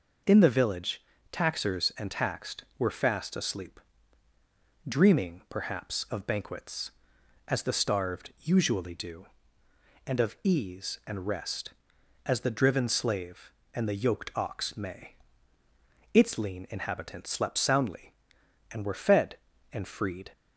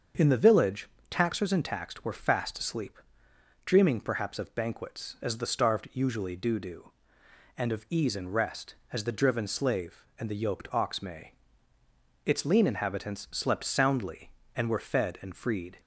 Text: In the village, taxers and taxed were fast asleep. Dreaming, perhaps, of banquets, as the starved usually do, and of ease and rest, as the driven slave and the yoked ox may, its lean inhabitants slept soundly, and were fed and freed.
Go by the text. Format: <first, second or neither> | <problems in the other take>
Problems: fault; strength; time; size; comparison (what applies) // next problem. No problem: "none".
first | starts louder than the rest; until 1.4 s; 6.5 dB // says "do" twice; at 6.5 s